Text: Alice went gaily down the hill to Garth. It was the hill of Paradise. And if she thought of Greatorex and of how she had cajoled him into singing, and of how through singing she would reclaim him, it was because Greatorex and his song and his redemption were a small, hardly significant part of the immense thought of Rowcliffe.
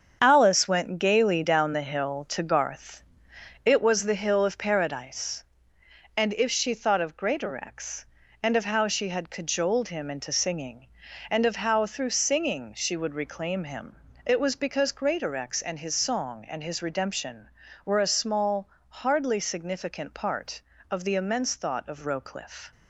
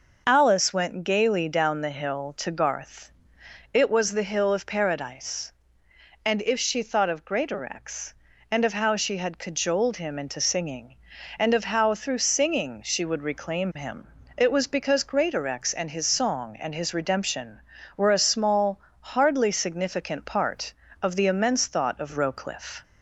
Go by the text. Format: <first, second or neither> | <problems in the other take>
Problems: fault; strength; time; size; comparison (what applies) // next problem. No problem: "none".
second | gets quieter; strong; throughout; 8.5 dB